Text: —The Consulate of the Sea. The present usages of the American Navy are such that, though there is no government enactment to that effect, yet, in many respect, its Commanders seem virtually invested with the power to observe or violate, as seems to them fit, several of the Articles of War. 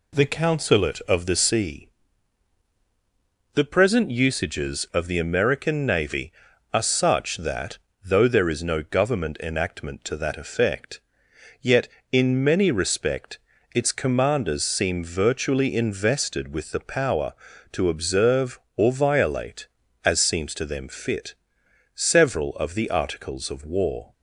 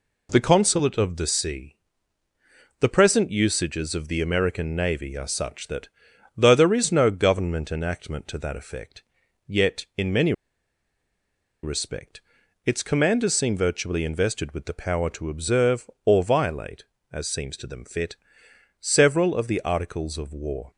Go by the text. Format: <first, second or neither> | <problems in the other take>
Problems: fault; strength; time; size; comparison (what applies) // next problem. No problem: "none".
first | pauses between "many" and "respect"; strong; at 10.3 s; 1.3 s long